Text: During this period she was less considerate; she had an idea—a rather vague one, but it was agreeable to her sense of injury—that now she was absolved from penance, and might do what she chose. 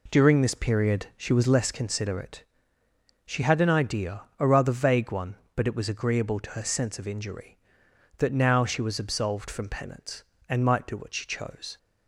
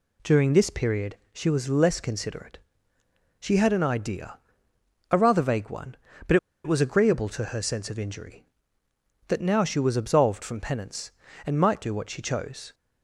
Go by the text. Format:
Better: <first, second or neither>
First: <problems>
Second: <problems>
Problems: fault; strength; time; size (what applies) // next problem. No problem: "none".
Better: first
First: none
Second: pauses between "period" and "she"; slight; at 1.1 s; 0.16 s long // pauses between "but" and "it"; slight; at 6.3 s; 0.27 s long